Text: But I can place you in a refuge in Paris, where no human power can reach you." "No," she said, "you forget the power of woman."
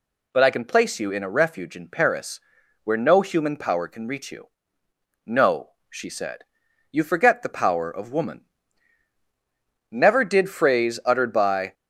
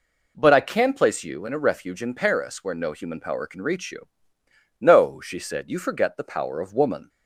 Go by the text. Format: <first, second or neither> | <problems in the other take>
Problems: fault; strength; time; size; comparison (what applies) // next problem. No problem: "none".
second | goes on to say "Never did phrase uttered by"; strong; from 9.8 s on; 1.8 s long